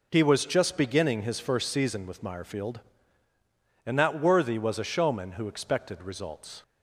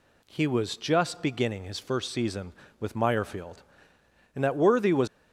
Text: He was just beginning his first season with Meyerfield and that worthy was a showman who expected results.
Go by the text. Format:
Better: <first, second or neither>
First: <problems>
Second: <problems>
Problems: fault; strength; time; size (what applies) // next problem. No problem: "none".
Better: first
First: none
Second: stops before "a showman who expected results"; at 5.0 s